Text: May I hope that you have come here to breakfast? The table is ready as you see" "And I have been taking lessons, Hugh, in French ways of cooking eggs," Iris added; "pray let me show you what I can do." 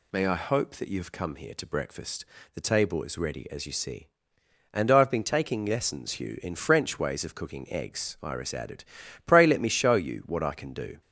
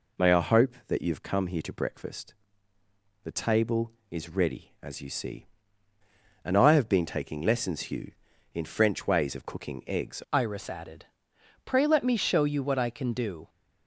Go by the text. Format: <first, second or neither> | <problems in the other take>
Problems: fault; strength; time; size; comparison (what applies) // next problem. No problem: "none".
first | changes voice at "Iris"; from 10.3 s on; 3.1 s long